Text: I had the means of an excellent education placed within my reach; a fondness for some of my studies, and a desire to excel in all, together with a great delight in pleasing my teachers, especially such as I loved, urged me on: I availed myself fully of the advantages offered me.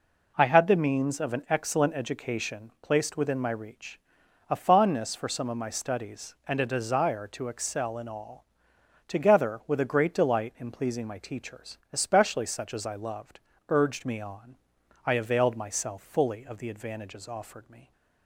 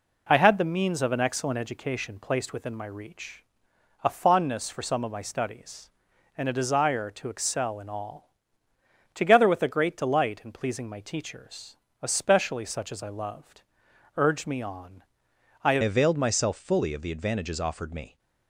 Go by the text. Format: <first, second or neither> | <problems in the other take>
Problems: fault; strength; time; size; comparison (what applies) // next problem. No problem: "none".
first | changes voice at "availed"; from 15.8 s on; 2.3 s long